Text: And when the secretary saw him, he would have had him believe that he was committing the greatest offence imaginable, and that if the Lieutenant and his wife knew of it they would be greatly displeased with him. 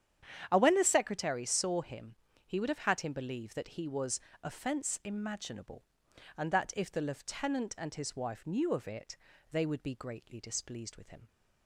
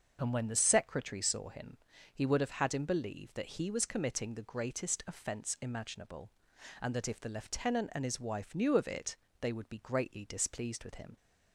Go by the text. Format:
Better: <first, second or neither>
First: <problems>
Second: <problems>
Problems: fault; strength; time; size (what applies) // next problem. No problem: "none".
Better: second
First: starts louder than the rest; strong; until 1.5 s; 9 dB // skips "committing the greatest"; at 4.3 s // pauses between "it" and "they"; slight; at 9.1 s; 0.36 s long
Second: starts louder than the rest; until 1.2 s; 6 dB // pauses between "it" and "they"; slight; at 9.1 s; 0.24 s long